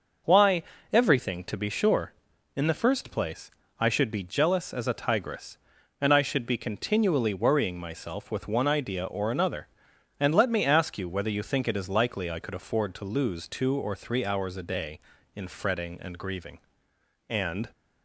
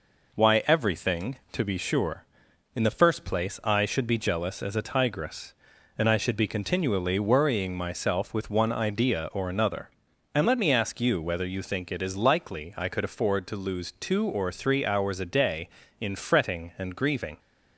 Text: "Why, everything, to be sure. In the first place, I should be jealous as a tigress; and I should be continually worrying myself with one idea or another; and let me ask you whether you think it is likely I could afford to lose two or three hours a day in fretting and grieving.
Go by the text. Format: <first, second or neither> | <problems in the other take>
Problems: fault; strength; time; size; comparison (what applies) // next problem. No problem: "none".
second | goes on to say "And"; slight; from 17.2 s on; 0.40 s long